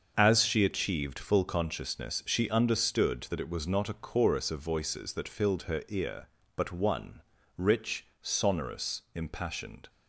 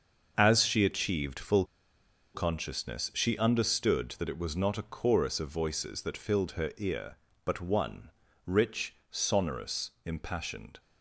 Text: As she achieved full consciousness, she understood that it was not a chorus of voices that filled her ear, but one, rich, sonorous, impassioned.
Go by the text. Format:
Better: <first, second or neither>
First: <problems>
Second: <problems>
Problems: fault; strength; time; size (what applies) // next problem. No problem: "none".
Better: first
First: starts louder than the rest; until 1.1 s; 6.5 dB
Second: starts louder than the rest; until 1.3 s; 6.5 dB // pauses between "full" and "consciousness"; noticeable; at 1.6 s; 0.70 s long